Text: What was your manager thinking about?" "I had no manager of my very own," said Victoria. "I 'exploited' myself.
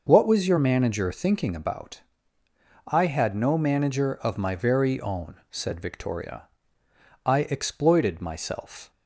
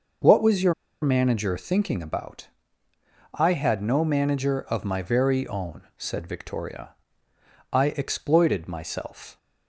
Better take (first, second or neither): first